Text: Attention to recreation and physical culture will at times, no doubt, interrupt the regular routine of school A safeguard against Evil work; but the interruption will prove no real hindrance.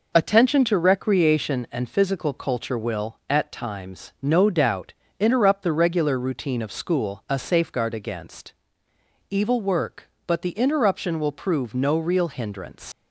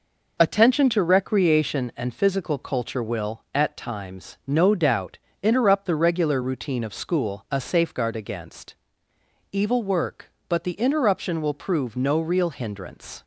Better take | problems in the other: second | pauses between "against" and "Evil"; noticeable; at 8.5 s; 0.76 s long; noticeable in the second // leaves "hindrance" unfinished; at 12.9 s; 95 ms

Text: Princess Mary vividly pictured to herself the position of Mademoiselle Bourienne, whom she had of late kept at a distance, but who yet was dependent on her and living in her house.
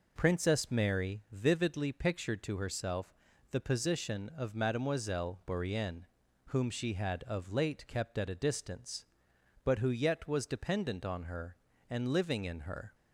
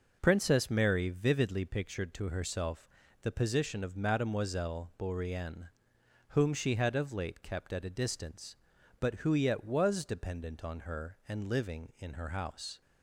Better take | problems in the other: second | pauses between "herself" and "the"; at 3.1 s; 0.38 s long; slight in the second // stops before "house"; at 12.9 s

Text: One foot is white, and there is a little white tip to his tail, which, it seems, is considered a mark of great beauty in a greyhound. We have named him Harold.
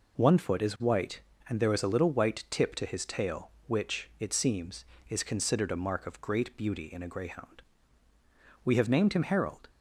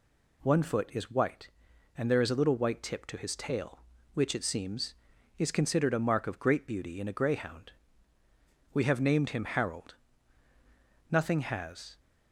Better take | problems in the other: first | goes on to say "Nothing has"; noticeable; from 11.0 s on; 0.90 s long

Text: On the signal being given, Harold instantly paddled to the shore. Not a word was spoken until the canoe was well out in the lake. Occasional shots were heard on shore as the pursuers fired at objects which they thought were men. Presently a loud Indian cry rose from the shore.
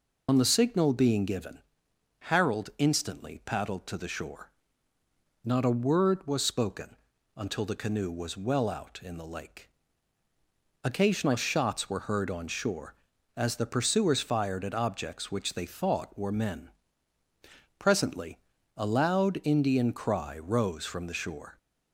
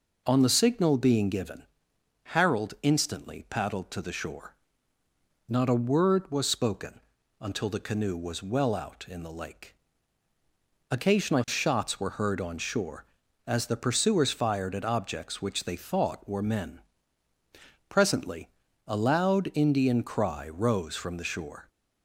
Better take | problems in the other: second | loses the start of "On"; at 0.2 s; 75 ms // pauses between "spoken" and "until"; at 6.9 s; 0.40 s long; also in the second // pauses between "Presently" and "a"; at 18.3 s; 0.40 s long; also in the second

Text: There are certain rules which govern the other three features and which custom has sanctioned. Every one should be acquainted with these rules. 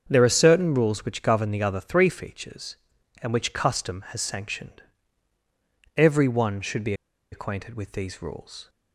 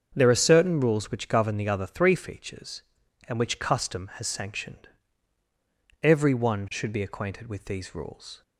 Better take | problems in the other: second | starts louder than the rest; strong; until 1.1 s; 7 dB; strong in the second // pauses between "be" and "acquainted"; at 6.9 s; 0.38 s long

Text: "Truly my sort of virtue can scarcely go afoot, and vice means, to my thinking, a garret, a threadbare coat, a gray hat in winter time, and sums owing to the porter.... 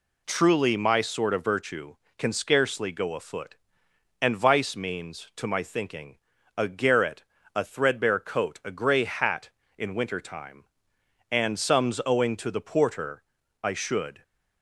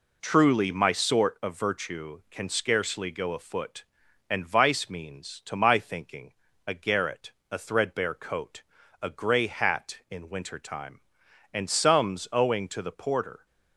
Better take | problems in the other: second | goes on to say "I should"; from 13.6 s on; 0.58 s long

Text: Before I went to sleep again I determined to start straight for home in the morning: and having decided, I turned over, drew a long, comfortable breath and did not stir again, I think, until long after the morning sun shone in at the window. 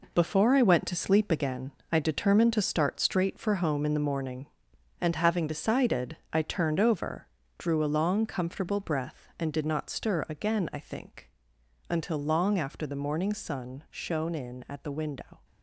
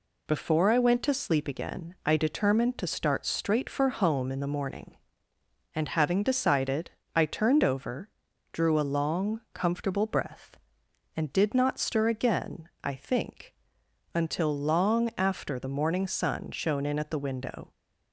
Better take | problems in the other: second | gets quieter; strong; throughout; 8.5 dB // pauses between "again" and "I"; slight; at 1.7 s; 0.20 s long

